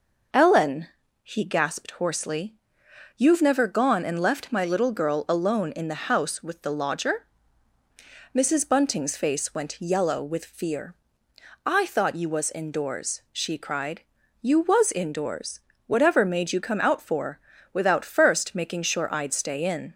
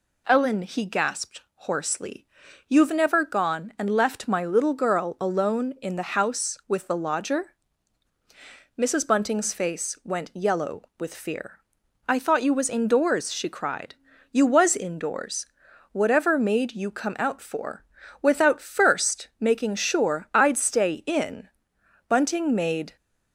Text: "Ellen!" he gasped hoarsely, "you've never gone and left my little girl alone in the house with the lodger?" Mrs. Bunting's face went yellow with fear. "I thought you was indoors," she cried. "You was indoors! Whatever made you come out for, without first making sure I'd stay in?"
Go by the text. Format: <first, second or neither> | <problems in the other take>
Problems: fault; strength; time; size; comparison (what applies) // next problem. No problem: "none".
first | goes on to say "Bunting made"; noticeable; from 22.0 s on; 0.86 s long